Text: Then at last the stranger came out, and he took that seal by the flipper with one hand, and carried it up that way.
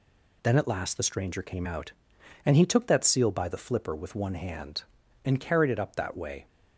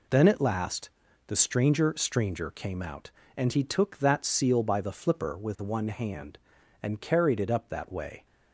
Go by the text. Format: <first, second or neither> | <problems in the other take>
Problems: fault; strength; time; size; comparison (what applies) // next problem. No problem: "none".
first | pauses between "last" and "the"; slight; at 0.8 s; 0.36 s long // says "stranger" twice; at 1.9 s